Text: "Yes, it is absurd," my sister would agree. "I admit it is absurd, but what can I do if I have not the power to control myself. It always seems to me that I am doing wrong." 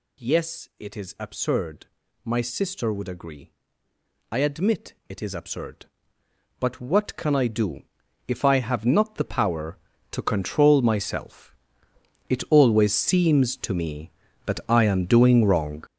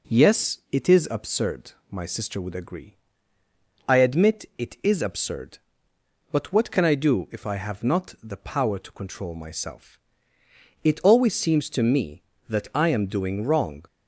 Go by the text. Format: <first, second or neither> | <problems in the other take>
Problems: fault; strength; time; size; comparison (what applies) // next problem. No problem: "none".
second | gets louder; strong; throughout; 9.5 dB // pauses between "do" and "if"; at 7.8 s; 0.44 s long